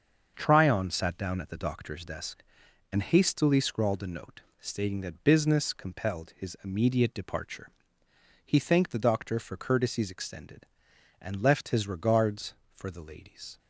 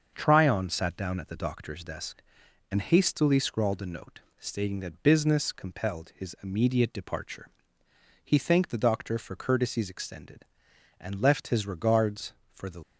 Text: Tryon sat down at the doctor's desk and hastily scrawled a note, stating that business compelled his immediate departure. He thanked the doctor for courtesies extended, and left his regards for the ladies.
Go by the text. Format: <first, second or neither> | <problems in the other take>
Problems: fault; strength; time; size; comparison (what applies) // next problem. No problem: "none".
first | starts louder than the rest; until 1.1 s; 6.5 dB; also in the first // stops before "ladies"; at 12.8 s